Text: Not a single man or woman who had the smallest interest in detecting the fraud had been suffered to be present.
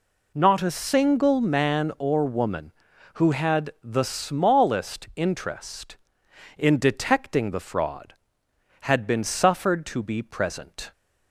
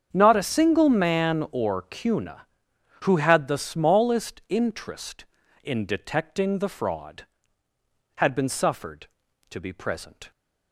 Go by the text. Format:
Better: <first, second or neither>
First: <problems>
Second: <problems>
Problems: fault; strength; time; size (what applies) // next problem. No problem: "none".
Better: first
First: none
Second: starts louder than the rest; strong; until 1.1 s; 7.5 dB // says "cuna" for "woman"; at 1.8 s